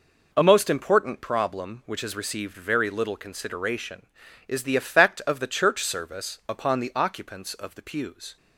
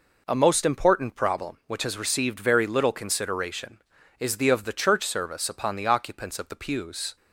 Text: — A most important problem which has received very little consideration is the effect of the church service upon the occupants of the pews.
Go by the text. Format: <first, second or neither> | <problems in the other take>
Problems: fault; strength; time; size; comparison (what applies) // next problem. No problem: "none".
first | skips "effect"; at 4.4 s